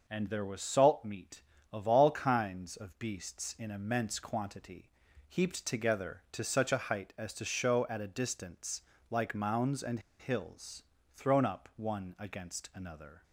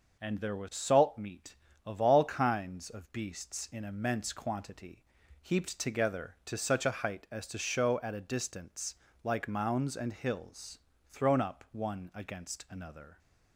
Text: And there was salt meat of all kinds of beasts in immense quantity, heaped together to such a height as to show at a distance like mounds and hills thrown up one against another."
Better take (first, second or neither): second